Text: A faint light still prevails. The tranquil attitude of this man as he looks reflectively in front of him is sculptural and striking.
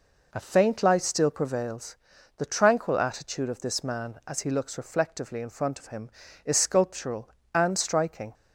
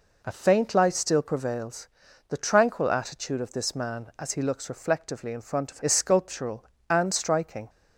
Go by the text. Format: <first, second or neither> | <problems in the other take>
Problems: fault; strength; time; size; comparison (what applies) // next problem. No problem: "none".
first | skips "him"; at 5.8 s